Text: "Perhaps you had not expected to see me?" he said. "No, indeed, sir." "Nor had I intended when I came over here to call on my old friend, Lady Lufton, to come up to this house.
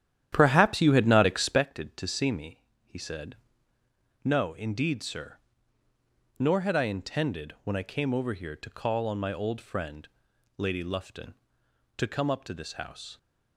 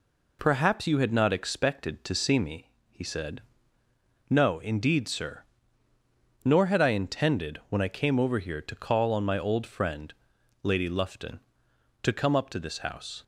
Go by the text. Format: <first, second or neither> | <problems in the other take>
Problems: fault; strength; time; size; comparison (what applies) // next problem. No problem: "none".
second | starts louder than the rest; strong; until 1.7 s; 11 dB